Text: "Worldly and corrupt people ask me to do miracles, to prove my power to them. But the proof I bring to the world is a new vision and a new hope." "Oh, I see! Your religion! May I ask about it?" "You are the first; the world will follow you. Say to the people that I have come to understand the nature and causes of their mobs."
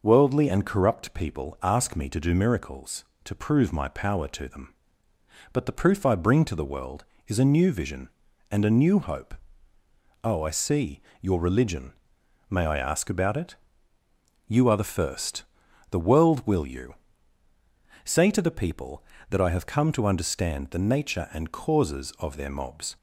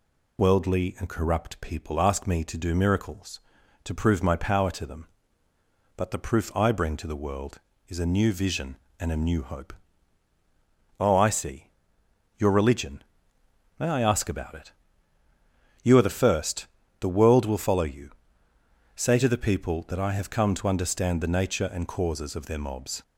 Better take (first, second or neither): second